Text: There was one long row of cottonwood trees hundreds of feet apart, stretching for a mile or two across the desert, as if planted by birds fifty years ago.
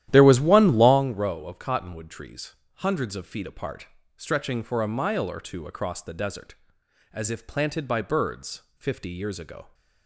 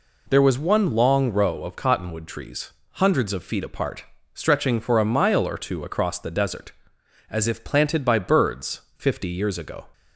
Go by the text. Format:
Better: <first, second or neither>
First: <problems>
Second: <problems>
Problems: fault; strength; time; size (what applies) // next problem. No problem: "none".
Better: second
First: starts louder than the rest; strong; until 1.0 s; 12.5 dB // pauses between "trees" and "hundreds"; slight; at 2.5 s; 0.20 s long // pauses between "birds" and "fifty"; slight; at 8.6 s; 0.16 s long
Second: pauses between "trees" and "hundreds"; slight; at 2.7 s; 0.20 s long // pauses between "birds" and "fifty"; slight; at 8.8 s; 0.16 s long